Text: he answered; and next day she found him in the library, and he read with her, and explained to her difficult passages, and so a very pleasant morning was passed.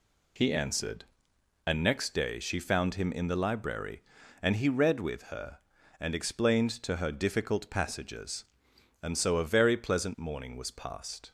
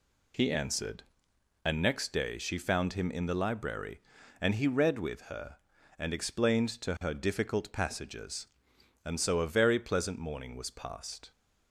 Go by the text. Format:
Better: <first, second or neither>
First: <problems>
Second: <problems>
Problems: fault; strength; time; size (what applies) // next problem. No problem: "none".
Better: neither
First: none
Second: none